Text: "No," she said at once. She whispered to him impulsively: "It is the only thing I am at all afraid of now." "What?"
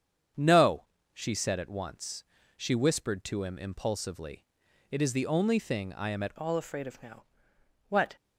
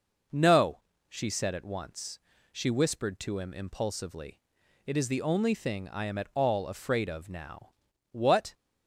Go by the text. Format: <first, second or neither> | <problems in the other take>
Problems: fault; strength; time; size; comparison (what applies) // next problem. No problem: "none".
second | starts louder than the rest; strong; until 1.6 s; 8 dB // changes voice at "all"; from 6.3 s on; 1.8 s long